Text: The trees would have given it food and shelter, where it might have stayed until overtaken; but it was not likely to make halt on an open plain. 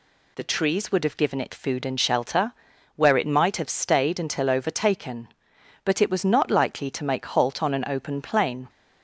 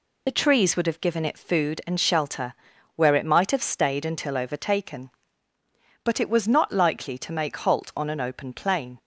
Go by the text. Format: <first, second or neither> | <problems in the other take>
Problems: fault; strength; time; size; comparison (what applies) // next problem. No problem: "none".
first | loses the start of "The"; at 0.2 s; 30 ms